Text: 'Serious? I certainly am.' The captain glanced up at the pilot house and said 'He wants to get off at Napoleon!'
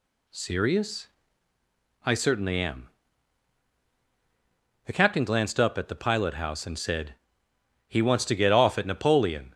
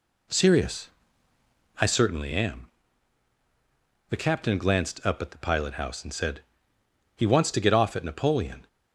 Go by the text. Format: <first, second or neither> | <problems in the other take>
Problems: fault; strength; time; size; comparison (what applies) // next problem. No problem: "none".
first | starts louder than the rest; slight; until 1.9 s; 2 dB // pauses between "said" and "He"; noticeable; at 6.4 s; 0.74 s long; noticeable in the first